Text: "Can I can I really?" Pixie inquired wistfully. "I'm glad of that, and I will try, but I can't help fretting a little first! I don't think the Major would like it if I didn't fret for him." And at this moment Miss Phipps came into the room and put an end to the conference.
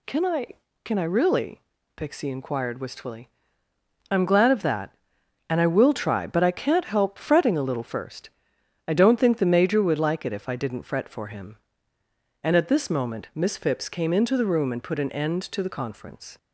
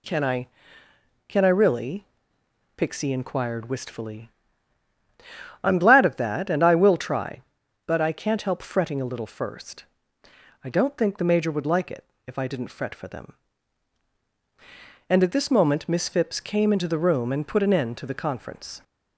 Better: first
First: none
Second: pauses between "it" and "if"; slight; at 12.0 s; 0.20 s long // says "them" for "him"; at 13.0 s

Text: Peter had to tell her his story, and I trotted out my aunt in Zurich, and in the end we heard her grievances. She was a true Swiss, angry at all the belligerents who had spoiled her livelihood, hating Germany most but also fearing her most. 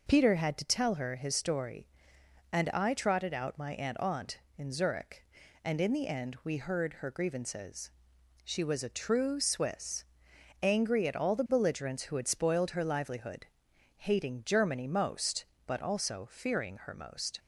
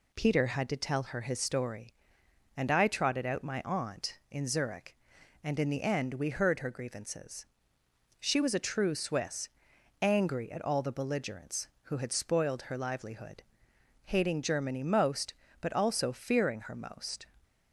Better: second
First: says "aunt" twice; at 3.9 s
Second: none

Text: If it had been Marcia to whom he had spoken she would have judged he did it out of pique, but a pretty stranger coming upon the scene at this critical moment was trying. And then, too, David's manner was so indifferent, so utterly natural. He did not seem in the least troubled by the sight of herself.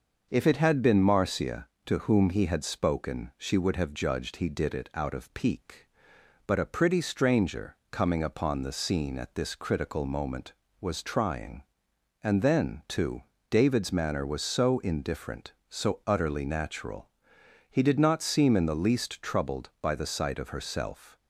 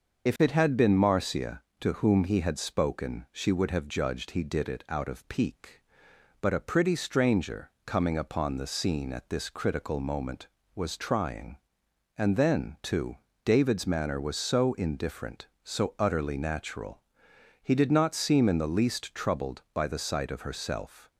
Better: first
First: starts louder than the rest; until 1.3 s; 6.5 dB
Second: loses the start of "If"; at 0.2 s; 40 ms // starts louder than the rest; until 1.3 s; 6 dB

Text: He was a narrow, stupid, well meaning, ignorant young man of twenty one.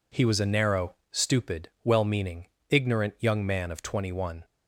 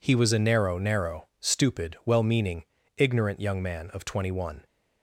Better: first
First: none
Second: says "narrow" twice; at 0.7 s

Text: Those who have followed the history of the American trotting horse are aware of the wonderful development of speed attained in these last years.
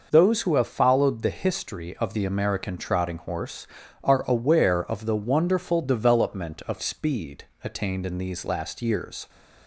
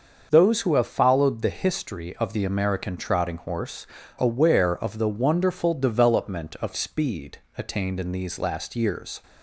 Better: first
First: pauses between "speed" and "attained"; slight; at 7.4 s; 0.18 s long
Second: starts louder than the rest; until 1.3 s; 6.5 dB // skips "are"; at 4.0 s // pauses between "speed" and "attained"; slight; at 7.3 s; 0.18 s long

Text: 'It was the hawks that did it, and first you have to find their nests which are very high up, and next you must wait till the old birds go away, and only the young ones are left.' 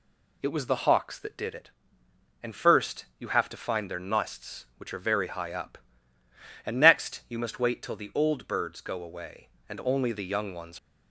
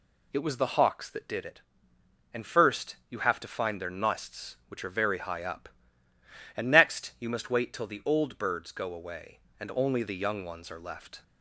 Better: second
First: stops before "are left"; at 10.7 s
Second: none

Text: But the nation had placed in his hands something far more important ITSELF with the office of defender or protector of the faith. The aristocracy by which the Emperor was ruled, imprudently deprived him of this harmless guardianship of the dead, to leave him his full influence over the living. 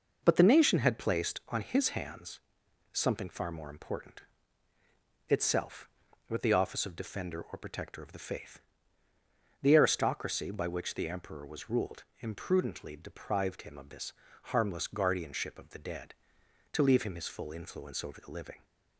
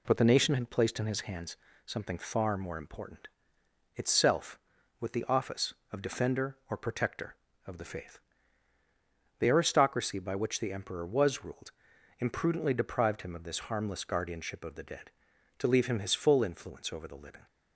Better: second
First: says "on" for "in"; at 1.4 s // pauses between "hands" and "something"; noticeable; at 2.3 s; 0.54 s long // pauses between "important" and "ITSELF"; at 4.2 s; 1.0 s long // pauses between "this" and "harmless"; slight; at 14.1 s; 0.32 s long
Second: pauses between "hands" and "something"; slight; at 1.5 s; 0.28 s long // pauses between "important" and "ITSELF"; noticeable; at 3.2 s; 0.70 s long

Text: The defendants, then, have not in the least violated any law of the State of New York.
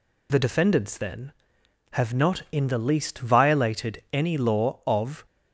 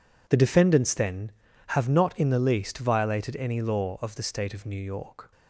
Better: second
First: stops before "the State of New York"; at 5.2 s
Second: none

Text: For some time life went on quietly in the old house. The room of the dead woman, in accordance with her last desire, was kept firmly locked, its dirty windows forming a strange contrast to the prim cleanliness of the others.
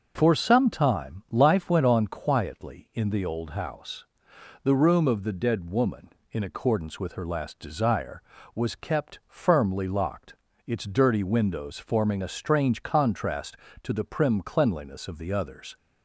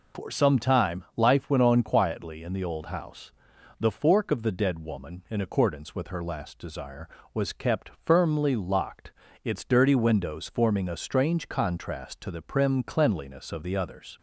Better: first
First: none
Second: says "fork" for "room"; at 3.9 s

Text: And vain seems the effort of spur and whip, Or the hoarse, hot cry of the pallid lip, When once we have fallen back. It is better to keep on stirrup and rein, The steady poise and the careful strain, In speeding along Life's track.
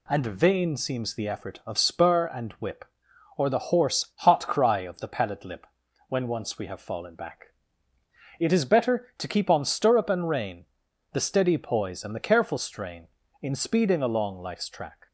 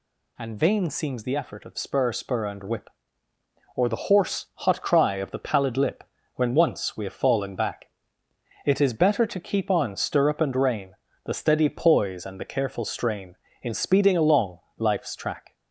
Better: first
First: none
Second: says "spur" twice; at 2.1 s // pauses between "along" and "Life's"; slight; at 14.5 s; 0.18 s long

